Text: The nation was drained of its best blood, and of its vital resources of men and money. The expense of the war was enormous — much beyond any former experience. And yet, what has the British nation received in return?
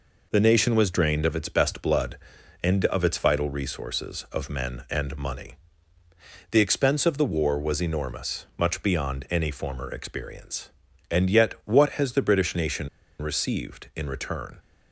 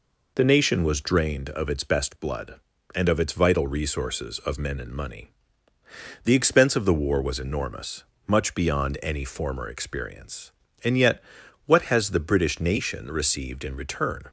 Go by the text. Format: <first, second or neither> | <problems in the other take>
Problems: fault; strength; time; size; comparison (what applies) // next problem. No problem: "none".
second | pauses between "nation" and "received"; slight; at 12.8 s; 0.32 s long